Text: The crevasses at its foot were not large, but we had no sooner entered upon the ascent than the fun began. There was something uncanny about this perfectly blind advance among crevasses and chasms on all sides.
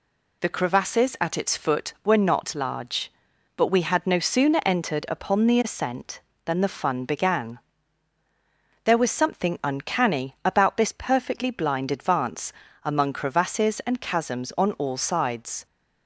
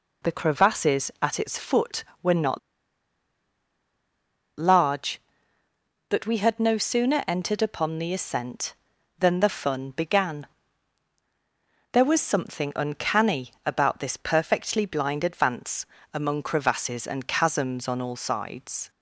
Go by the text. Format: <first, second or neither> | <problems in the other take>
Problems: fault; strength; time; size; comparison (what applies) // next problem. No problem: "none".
first | pauses between "not" and "large"; strong; at 2.5 s; 1.9 s long // pauses between "advance" and "among"; slight; at 15.8 s; 0.26 s long; slight in the first